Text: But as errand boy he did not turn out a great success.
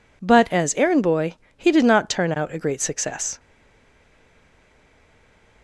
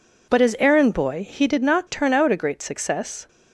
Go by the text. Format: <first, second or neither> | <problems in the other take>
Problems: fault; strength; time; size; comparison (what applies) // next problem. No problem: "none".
second | pauses between "boy" and "he"; slight; at 1.3 s; 0.24 s long // stays silent after the last word; from 3.3 s on; 2.3 s long